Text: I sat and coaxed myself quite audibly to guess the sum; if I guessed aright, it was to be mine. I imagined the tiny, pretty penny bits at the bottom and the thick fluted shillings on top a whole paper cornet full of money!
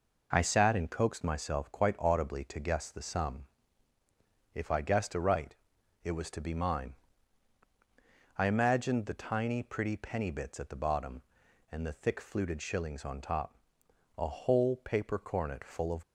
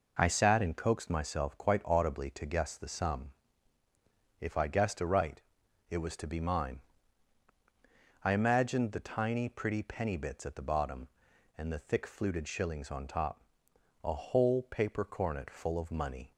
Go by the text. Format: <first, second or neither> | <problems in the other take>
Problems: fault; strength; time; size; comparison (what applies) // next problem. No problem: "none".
second | pauses between "top" and "a"; noticeable; at 13.5 s; 0.60 s long; noticeable in the second // stops before "money"; at 16.0 s